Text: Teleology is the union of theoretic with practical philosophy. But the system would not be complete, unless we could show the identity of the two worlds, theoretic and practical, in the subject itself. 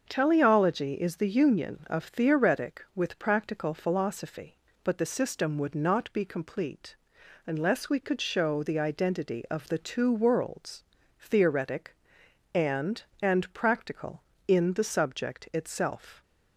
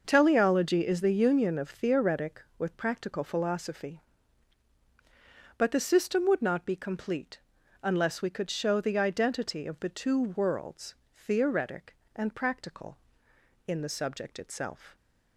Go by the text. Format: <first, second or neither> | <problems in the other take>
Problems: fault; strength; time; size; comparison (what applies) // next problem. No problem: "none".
second | starts louder than the rest; until 1.0 s; 6.5 dB; noticeable in the second // says "and" twice; at 13.2 s